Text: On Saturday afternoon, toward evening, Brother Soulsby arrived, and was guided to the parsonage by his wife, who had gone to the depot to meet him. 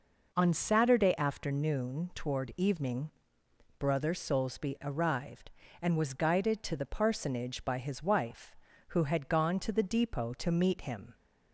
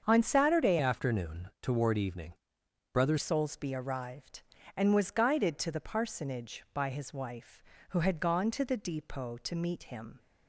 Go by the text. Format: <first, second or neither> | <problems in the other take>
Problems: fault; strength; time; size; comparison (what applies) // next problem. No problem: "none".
first | starts louder than the rest; until 1.0 s; 7 dB // changes voice from "afternoon" to "Brother"; from 0.7 to 3.1 s; 2.4 s long